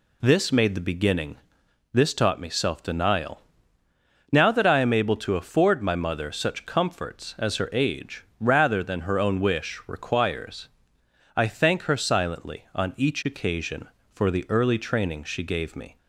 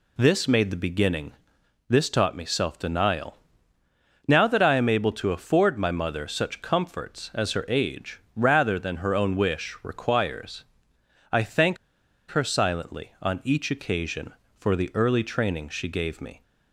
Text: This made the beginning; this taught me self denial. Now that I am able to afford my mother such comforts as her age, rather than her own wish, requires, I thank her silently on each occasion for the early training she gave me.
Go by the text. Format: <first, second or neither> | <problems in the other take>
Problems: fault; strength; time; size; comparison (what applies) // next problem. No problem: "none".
first | pauses between "thank" and "her"; noticeable; at 11.7 s; 0.53 s long